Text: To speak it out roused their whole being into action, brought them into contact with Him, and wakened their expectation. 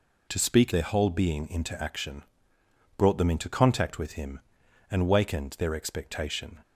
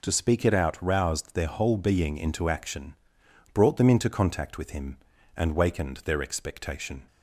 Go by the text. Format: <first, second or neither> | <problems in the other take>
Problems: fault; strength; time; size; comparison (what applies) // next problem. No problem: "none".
second | skips "it out roused"; at 0.7 s